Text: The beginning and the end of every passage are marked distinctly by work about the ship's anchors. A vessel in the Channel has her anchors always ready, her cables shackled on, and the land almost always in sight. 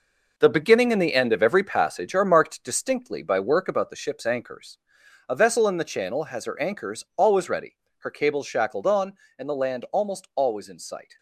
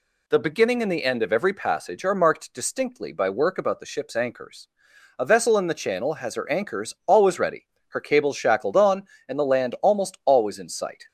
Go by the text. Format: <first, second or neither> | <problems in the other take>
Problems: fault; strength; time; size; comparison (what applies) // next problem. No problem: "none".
second | gets quieter; strong; throughout; 8 dB